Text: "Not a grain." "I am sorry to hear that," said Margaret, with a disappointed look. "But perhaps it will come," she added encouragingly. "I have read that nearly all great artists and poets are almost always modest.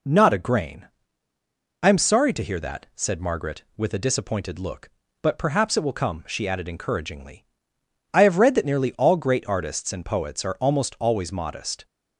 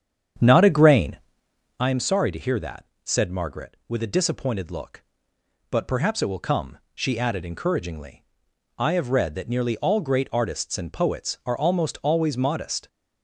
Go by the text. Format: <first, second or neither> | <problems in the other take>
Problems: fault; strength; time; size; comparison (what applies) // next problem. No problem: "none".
first | starts louder than the rest; strong; until 1.9 s; 8 dB